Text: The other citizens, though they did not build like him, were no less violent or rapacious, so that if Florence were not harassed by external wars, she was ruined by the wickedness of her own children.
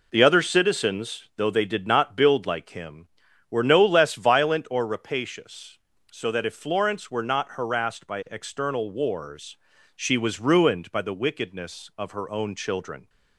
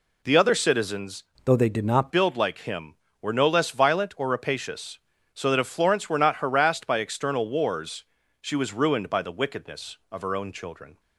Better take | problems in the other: first | changes voice from "though" to "not"; from 1.4 to 2.1 s; 0.7 s long

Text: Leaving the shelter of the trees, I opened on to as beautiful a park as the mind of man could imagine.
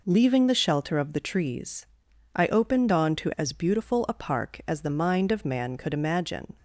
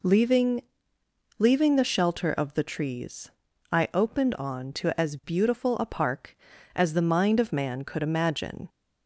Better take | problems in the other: first | says "Leaving" twice; at 1.3 s

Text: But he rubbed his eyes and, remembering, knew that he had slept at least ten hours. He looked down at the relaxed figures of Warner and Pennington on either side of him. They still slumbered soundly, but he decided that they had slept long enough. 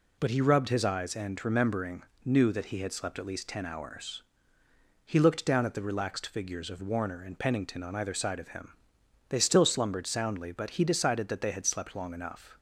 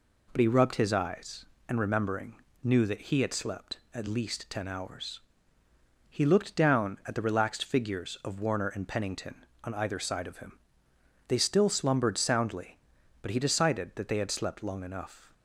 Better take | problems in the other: neither | none

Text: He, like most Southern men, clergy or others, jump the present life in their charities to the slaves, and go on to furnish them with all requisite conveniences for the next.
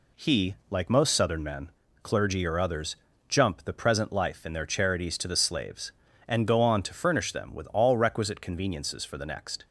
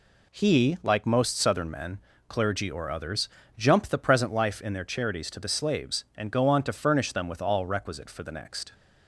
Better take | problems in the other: first | skips "conveniences"; at 8.1 s

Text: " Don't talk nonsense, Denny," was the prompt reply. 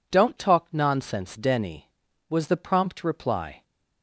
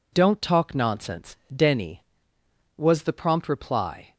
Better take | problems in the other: neither | none

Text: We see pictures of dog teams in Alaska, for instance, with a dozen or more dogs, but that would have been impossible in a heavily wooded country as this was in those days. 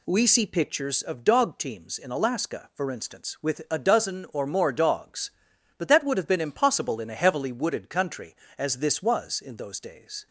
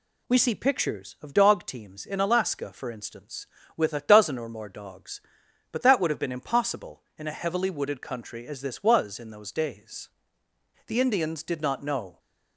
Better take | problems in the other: first | goes on to say "The Indians did not know"; from 10.8 s on; 1.3 s long

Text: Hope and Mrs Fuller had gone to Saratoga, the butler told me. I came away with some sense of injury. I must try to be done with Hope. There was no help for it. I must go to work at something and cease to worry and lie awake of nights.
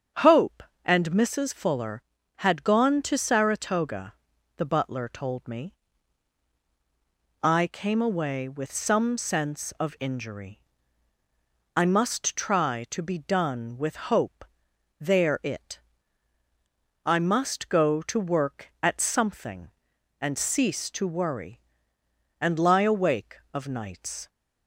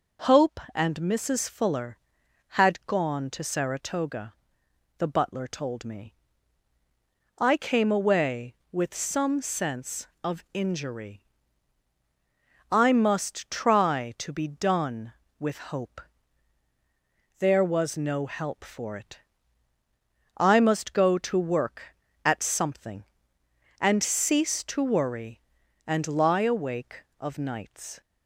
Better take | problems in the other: second | starts louder than the rest; strong; until 1.4 s; 7.5 dB // skips "was no help for"; at 15.4 s

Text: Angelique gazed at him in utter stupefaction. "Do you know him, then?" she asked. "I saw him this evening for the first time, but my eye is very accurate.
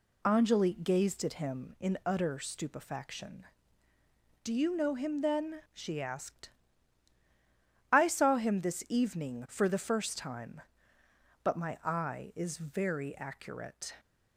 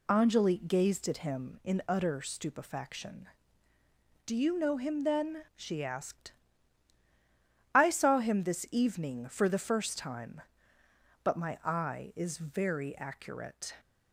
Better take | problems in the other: neither | none

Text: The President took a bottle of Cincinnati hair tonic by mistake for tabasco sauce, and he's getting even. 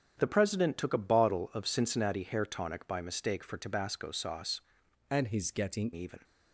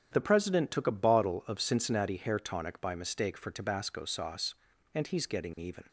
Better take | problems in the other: second | starts louder than the rest; strong; until 1.1 s; 7.5 dB; strong in the second // changes voice from "and" to "getting"; from 5.1 to 5.9 s; 0.8 s long

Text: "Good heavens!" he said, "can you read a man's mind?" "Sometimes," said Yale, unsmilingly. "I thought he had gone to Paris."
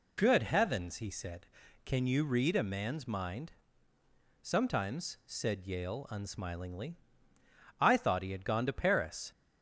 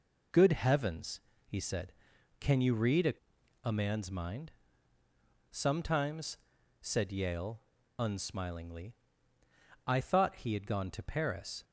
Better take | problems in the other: first | says "a" twice; at 3.6 s

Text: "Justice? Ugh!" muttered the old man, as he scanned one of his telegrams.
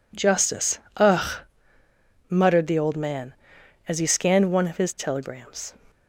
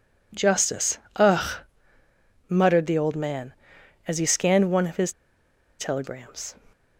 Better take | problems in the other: first | pauses between "his" and "telegrams"; noticeable; at 5.1 s; 0.66 s long

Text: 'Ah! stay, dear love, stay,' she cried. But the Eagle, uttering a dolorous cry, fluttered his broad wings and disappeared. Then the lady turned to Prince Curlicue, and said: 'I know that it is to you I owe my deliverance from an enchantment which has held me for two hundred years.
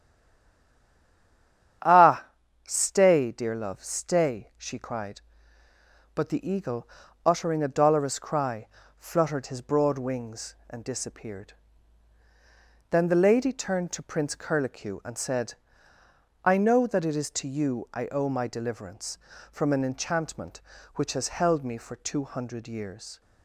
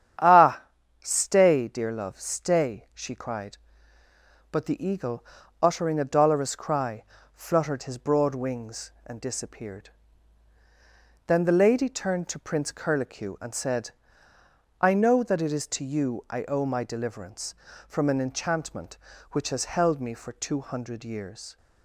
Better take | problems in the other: second | stays silent before the first word; noticeable; until 1.8 s; 1.8 s long // starts louder than the rest; strong; until 3.2 s; 9.5 dB; strong in the second

